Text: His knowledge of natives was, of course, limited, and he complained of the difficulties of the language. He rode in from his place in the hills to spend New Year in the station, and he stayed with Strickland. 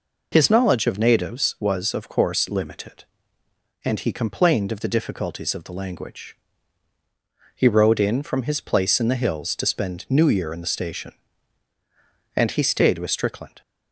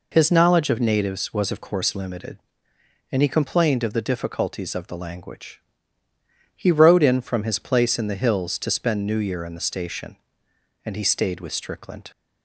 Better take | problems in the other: neither | none

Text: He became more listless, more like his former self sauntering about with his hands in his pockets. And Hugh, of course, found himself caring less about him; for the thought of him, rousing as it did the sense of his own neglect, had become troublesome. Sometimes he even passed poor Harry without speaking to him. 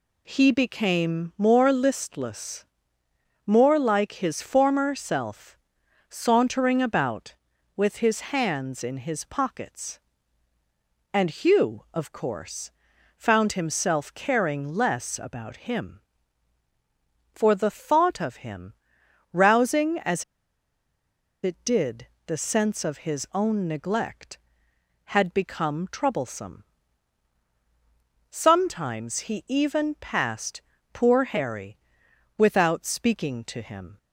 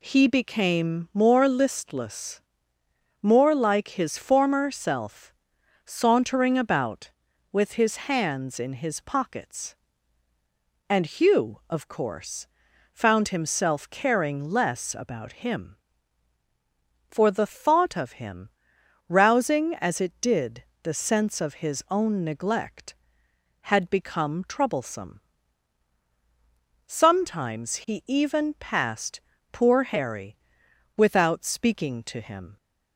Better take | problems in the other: second | pauses between "self" and "sauntering"; noticeable; at 5.5 s; 0.54 s long; noticeable in the second // pauses between "as" and "it"; at 20.2 s; 1.1 s long // pauses between "did" and "the"; slight; at 22.0 s; 0.18 s long; slight in the second // pauses between "passed" and "poor"; slight; at 30.6 s; 0.32 s long; slight in the second // pauses between "Harry" and "without"; noticeable; at 31.7 s; 0.62 s long; noticeable in the second

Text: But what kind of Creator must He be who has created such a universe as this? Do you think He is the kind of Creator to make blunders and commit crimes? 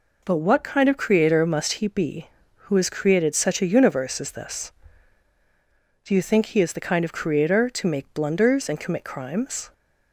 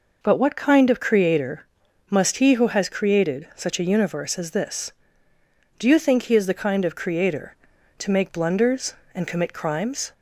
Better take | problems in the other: first | pauses between "Creator" and "must"; noticeable; at 1.6 s; 0.46 s long // skips "be"; at 2.5 s

